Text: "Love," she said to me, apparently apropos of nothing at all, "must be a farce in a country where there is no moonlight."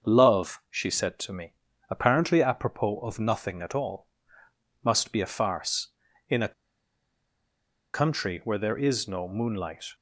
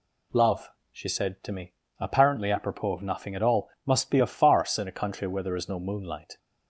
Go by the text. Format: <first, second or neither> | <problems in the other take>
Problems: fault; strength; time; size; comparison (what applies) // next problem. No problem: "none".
second | starts louder than the rest; until 1.1 s; 6.5 dB // pauses between "a" and "country"; strong; at 6.5 s; 1.4 s long